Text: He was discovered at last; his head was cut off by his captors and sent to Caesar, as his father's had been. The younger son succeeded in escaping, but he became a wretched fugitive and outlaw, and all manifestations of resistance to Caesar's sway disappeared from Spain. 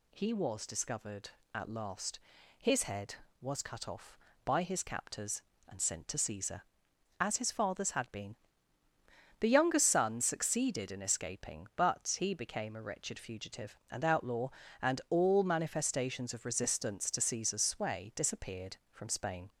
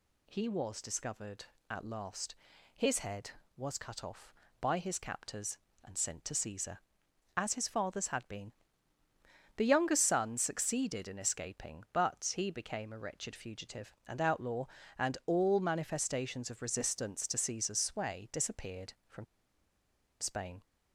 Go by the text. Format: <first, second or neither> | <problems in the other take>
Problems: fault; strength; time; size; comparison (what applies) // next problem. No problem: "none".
first | pauses between "from" and "Spain"; noticeable; at 19.2 s; 0.95 s long